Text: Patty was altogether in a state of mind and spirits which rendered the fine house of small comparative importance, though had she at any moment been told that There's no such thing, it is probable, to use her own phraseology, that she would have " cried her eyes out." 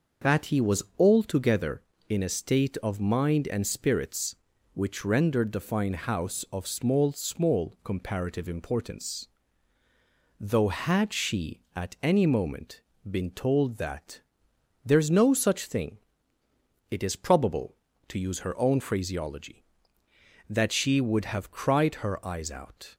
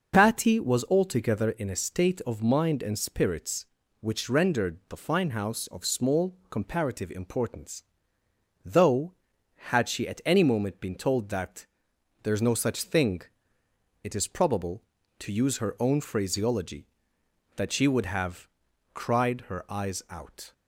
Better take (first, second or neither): second